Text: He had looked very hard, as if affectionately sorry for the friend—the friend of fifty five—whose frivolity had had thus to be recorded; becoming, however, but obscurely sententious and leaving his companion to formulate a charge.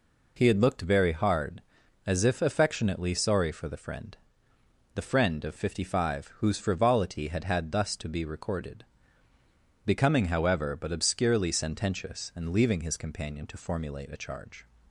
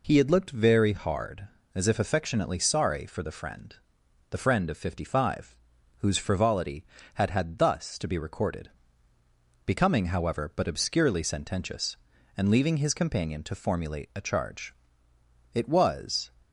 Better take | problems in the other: first | goes on to say "It was"; noticeable; from 15.5 s on; 0.74 s long

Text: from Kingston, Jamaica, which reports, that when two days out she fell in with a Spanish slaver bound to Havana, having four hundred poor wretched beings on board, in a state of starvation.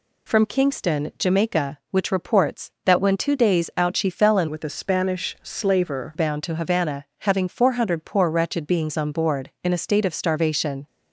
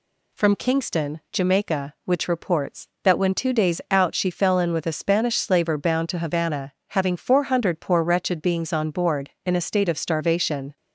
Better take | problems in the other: second | changes voice from "with" to "slaver"; from 4.4 to 6.1 s; 1.7 s long

